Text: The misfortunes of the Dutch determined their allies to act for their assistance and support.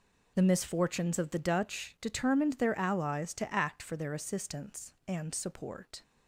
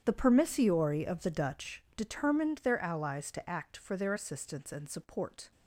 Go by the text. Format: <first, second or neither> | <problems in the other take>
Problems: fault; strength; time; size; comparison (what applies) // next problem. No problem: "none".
first | starts louder than the rest; strong; until 1.0 s; 9 dB // says "permissiori" for "misfortunes"; at 0.1 s